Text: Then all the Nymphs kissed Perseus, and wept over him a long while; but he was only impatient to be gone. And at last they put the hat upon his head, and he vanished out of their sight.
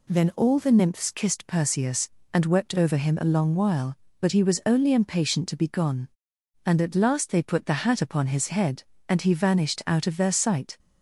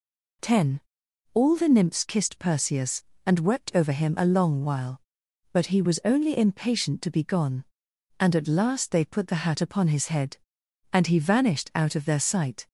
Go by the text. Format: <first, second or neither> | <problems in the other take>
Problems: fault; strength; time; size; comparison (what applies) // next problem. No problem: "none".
first | says "Ten" for "Then"; at 0.4 s